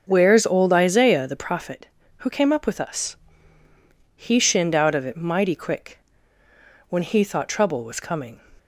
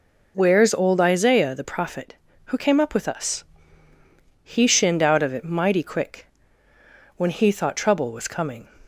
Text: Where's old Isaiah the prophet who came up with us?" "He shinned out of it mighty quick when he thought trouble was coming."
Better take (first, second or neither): second